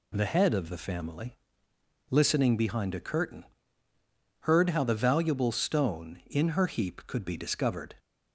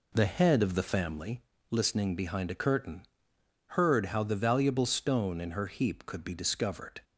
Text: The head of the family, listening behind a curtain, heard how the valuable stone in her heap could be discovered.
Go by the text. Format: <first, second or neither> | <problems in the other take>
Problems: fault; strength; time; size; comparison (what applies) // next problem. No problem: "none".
first | starts louder than the rest; slight; until 1.3 s; 3.5 dB